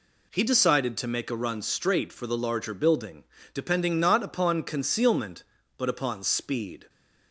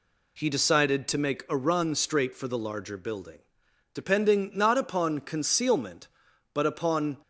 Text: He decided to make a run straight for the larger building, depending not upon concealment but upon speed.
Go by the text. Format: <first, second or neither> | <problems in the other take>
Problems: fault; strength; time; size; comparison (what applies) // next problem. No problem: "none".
first | stops before "speed"; at 7.2 s